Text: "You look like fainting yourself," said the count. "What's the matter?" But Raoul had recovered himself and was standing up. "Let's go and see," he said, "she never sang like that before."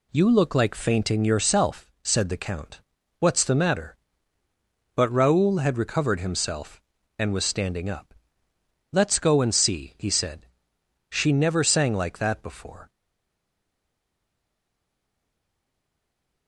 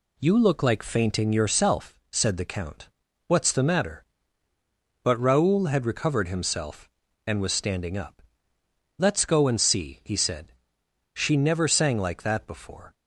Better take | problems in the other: second | stays silent after the last word; strong; from 12.8 s on; 3.6 s long

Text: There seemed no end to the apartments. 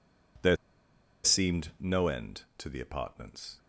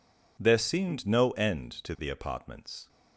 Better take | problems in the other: second | pauses between "There" and "seemed"; noticeable; at 0.5 s; 0.67 s long

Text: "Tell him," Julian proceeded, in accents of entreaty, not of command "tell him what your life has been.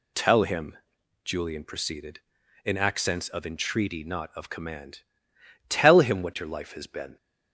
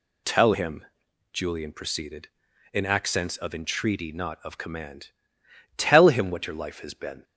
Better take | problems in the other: neither | pauses between "command" and "tell"; noticeable; the same in both

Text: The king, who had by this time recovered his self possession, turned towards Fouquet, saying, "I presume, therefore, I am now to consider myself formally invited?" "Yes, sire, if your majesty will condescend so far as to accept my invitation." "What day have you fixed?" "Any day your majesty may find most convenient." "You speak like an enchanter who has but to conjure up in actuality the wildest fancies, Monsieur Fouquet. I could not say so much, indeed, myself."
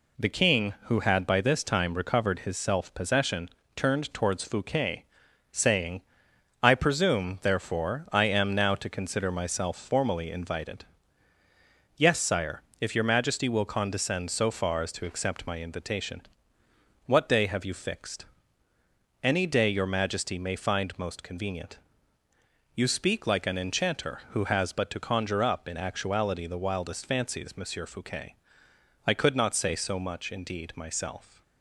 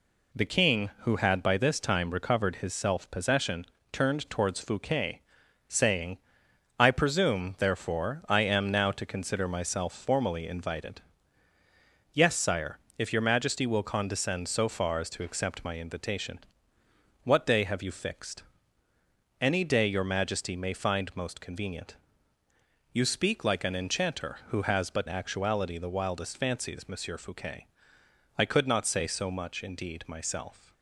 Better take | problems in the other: first | skips "to conjure up in"; at 25.0 s

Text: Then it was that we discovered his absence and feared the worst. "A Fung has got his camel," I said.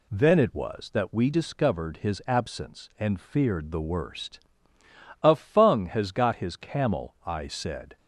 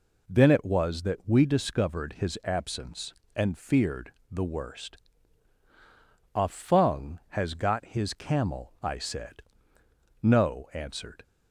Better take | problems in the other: first | pauses between "feared" and "the"; slight; at 4.1 s; 0.20 s long // goes on to say "No answered"; noticeable; from 10.2 s on; 1.0 s long

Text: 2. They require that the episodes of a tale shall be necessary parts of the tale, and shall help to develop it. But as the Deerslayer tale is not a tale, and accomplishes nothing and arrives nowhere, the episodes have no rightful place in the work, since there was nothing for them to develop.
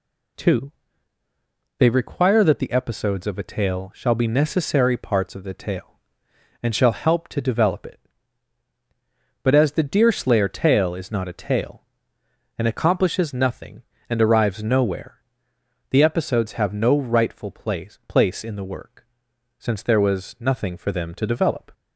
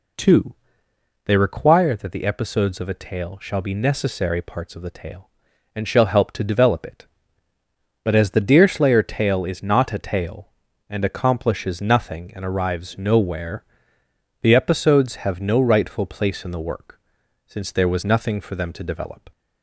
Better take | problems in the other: second | says "place" twice; at 18.0 s

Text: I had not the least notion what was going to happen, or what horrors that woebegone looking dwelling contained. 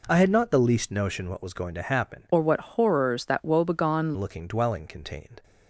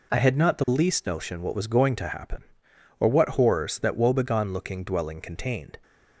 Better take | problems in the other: second | changes voice from "or" to "woebegone"; from 2.3 to 4.1 s; 1.8 s long

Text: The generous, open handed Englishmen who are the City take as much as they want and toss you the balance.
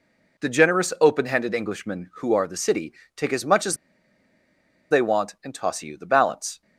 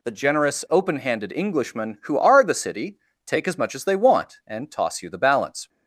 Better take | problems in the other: second | pauses between "City" and "take"; slight; at 2.9 s; 0.22 s long; slight in the second // pauses between "as" and "they"; at 3.7 s; 1.1 s long

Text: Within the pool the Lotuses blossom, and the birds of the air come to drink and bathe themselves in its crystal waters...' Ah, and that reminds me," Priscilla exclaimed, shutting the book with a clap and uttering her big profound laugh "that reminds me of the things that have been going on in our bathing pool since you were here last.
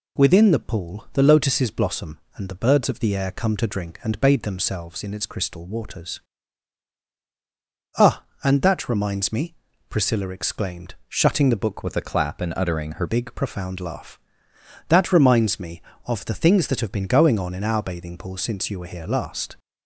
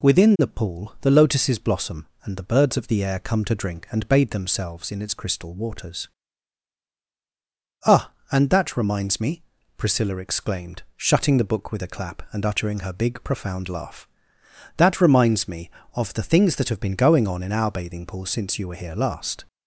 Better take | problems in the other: second | changes voice from "with" to "her"; from 11.8 to 13.0 s; 1.2 s long

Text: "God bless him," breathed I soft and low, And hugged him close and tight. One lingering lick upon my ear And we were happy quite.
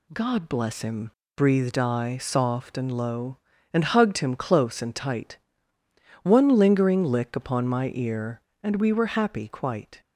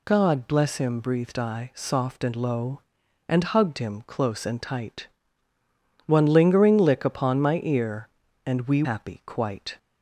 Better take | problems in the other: first | skips "were"; at 8.8 s

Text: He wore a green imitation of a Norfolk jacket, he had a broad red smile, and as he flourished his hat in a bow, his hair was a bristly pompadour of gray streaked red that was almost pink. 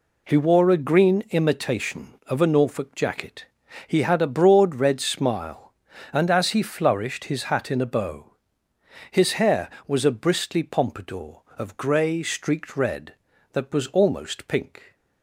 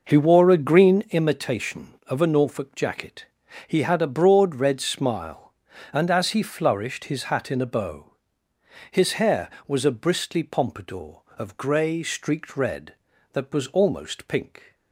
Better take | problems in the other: first | starts louder than the rest; noticeable; until 1.3 s; 5.5 dB

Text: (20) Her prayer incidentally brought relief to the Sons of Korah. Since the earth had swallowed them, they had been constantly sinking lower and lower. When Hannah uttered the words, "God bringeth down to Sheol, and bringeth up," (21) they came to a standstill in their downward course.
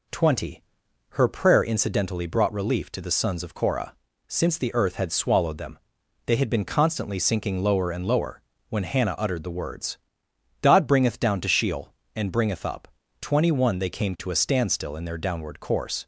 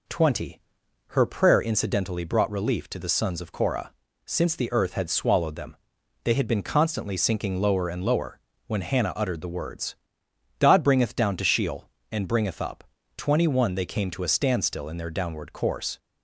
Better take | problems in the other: neither | none

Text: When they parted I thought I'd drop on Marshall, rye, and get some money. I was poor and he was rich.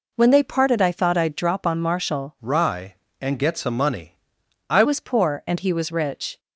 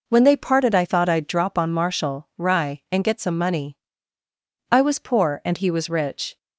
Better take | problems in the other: second | changes voice from "rye" to "I"; from 2.4 to 4.8 s; 2.4 s long

